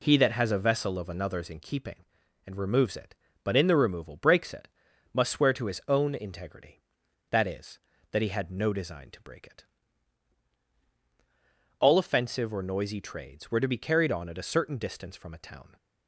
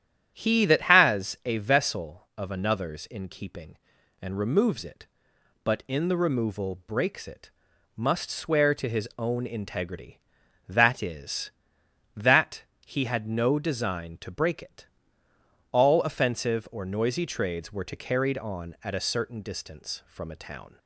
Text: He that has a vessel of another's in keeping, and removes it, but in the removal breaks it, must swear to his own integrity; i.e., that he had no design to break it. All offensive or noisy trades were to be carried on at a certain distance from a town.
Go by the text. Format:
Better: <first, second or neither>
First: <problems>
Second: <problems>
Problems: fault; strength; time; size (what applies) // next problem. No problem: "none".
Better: first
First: none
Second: starts louder than the rest; strong; until 1.3 s; 10 dB // pauses between "that" and "he"; slight; at 12.6 s; 0.20 s long // skips "be"; at 17.9 s